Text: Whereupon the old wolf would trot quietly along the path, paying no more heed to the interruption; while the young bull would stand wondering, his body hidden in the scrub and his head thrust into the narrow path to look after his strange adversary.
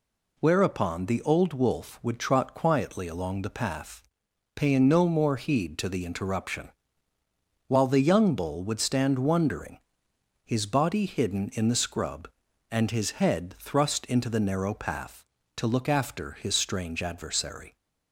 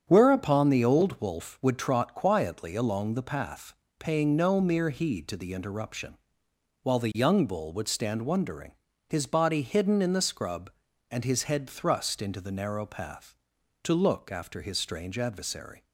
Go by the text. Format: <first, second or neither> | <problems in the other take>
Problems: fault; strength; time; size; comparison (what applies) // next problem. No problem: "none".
first | starts louder than the rest; strong; until 1.0 s; 8 dB // says "mere" for "more"; at 4.5 s